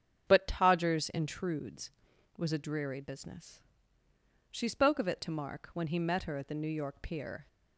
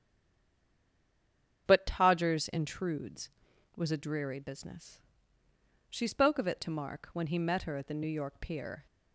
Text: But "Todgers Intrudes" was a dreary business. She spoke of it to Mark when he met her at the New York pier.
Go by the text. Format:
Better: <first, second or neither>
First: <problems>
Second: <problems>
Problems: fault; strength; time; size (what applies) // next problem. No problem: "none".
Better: first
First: starts louder than the rest; strong; until 1.3 s; 8 dB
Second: stays silent before the first word; noticeable; until 1.6 s; 1.6 s long // starts louder than the rest; strong; until 2.6 s; 7.5 dB